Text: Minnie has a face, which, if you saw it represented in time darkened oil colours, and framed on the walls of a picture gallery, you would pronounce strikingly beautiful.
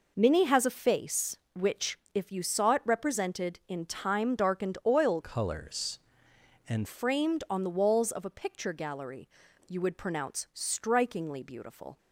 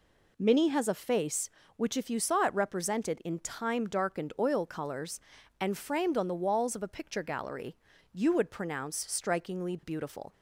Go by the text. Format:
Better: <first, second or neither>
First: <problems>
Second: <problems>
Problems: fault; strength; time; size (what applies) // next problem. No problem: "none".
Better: second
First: changes voice from "colours" to "and"; from 5.2 to 6.8 s; 1.6 s long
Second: none